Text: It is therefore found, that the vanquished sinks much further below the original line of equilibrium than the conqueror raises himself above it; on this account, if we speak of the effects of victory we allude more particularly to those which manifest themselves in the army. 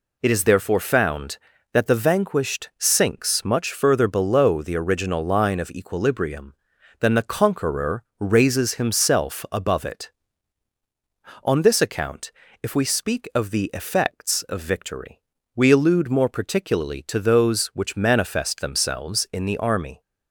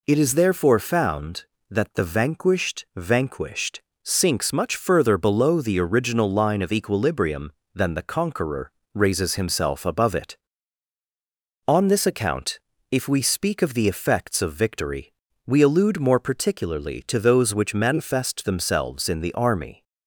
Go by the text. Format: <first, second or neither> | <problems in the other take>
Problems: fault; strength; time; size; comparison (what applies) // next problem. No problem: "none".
first | says "vanquished" twice; at 2.9 s // pauses between "conqueror" and "raises"; slight; at 8.7 s; 0.22 s long; slight in the first // pauses between "victory" and "we"; slight; at 15.1 s; 0.32 s long; slight in the first